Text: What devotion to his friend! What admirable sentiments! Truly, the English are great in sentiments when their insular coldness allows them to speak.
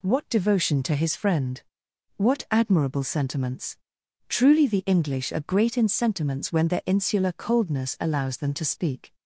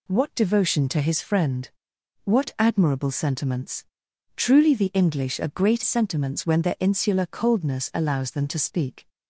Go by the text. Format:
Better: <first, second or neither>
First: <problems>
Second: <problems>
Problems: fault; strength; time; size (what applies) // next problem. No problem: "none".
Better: first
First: none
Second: skips "in"; at 5.8 s